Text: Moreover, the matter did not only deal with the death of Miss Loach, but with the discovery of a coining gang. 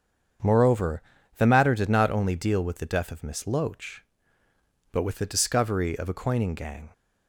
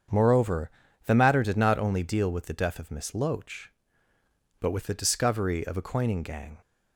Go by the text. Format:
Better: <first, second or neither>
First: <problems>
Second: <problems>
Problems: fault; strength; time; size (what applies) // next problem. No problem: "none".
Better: neither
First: starts louder than the rest; strong; until 1.7 s; 7.5 dB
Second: starts louder than the rest; strong; until 1.4 s; 7.5 dB